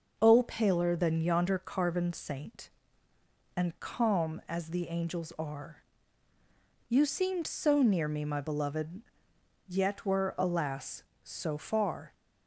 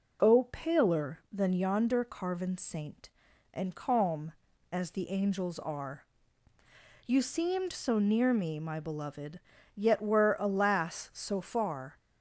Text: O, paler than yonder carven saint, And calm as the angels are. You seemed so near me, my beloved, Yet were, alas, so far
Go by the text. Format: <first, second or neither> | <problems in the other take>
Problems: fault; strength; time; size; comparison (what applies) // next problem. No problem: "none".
neither | none